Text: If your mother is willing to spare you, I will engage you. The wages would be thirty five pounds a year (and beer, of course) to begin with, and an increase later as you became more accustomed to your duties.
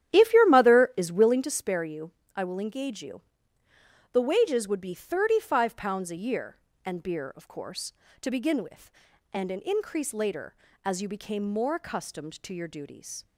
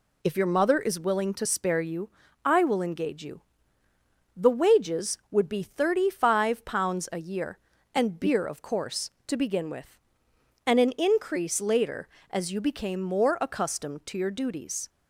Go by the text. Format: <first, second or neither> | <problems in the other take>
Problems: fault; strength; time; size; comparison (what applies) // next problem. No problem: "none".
second | starts louder than the rest; strong; until 1.5 s; 11 dB